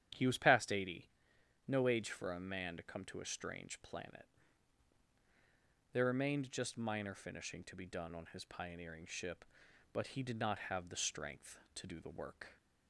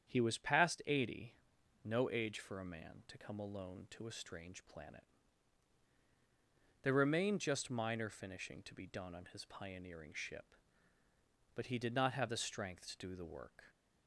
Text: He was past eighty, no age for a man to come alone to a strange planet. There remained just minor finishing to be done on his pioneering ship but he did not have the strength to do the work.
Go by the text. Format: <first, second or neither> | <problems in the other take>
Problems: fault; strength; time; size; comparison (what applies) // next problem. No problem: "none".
second | starts louder than the rest; strong; until 1.7 s; 10 dB; strong in the second // skips "alone"; at 3.0 s